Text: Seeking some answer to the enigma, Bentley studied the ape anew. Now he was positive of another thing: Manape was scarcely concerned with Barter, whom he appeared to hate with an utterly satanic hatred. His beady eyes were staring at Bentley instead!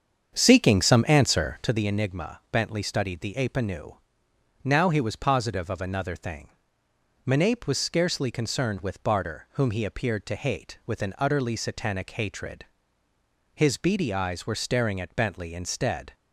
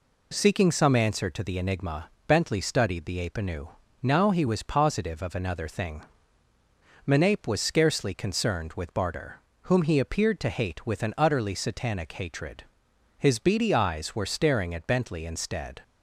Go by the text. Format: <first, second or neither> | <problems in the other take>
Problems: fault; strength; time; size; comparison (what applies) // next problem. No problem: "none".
second | starts louder than the rest; strong; until 1.8 s; 7.5 dB